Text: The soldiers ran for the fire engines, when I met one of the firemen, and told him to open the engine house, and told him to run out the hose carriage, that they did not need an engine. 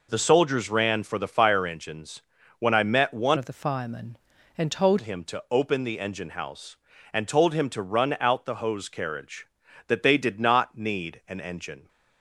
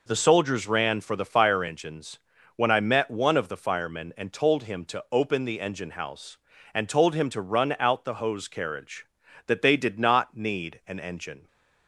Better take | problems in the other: second | changes voice from "of" to "told"; from 3.3 to 4.9 s; 1.6 s long

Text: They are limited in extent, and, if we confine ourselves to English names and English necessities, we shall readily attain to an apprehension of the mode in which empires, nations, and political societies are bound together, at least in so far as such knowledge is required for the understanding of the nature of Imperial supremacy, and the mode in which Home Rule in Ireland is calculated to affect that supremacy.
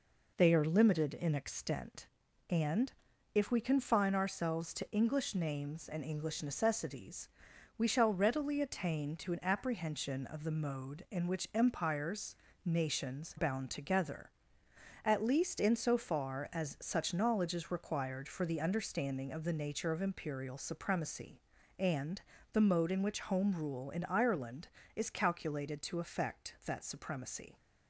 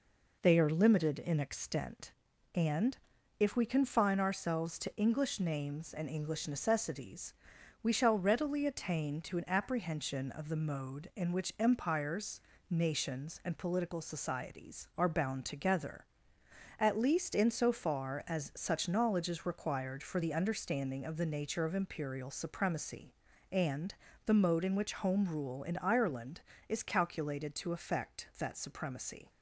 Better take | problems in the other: second | skips "and political societies are"; at 13.3 s // pauses between "and" and "the"; slight; at 22.2 s; 0.32 s long; slight in the second

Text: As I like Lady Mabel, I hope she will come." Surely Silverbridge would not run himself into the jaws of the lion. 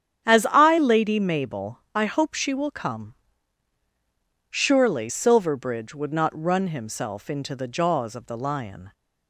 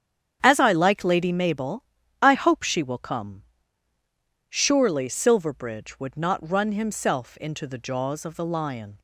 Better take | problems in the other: second | starts louder than the rest; strong; until 1.3 s; 9 dB; strong in the second // skips "like"; at 0.7 s

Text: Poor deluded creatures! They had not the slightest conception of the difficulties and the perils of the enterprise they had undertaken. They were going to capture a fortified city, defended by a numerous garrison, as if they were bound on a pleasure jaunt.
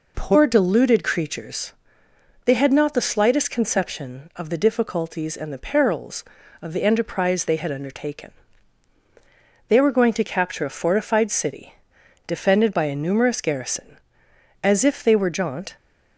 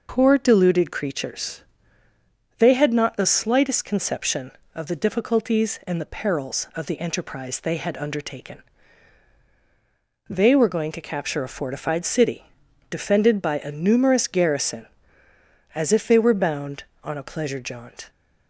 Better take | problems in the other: second | skips "bound on a pleasure"; at 15.2 s

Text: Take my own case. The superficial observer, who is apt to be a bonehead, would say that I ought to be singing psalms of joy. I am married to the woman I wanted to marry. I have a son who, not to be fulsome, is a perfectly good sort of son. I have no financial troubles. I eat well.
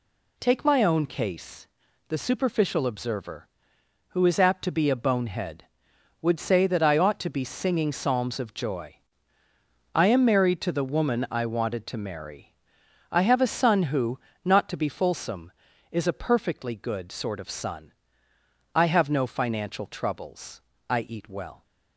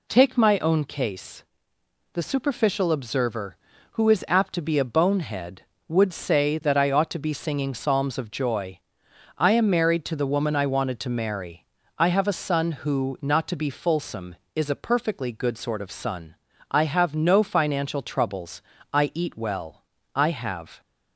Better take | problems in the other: first | goes on to say "I have"; noticeable; from 20.1 s on; 0.66 s long

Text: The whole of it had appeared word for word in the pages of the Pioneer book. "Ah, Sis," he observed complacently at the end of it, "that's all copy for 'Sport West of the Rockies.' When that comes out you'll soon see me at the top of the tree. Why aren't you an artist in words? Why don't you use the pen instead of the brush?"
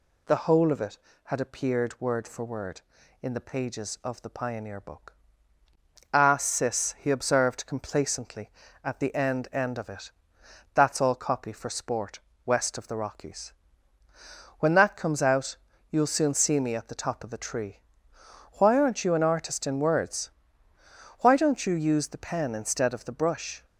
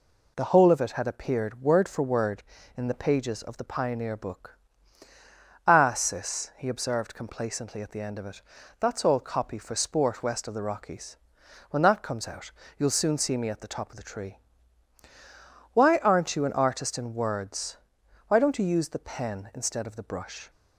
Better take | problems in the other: second | says "end" twice; at 9.5 s // pauses between "Sport" and "West"; slight; at 12.1 s; 0.26 s long // pauses between "out" and "you'll"; slight; at 15.5 s; 0.32 s long; slight in the second

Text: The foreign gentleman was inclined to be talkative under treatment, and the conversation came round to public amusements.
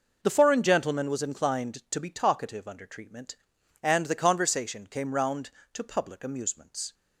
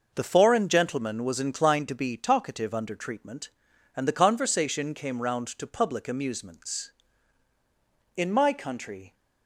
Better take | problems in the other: first | goes on to say "In my country"; noticeable; from 8.1 s on; 1.0 s long

